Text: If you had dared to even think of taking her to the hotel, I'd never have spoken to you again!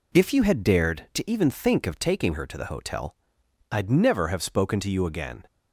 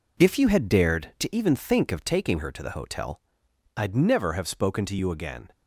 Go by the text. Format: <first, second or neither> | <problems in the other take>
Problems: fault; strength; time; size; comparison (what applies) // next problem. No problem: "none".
first | gets quieter; throughout; 6 dB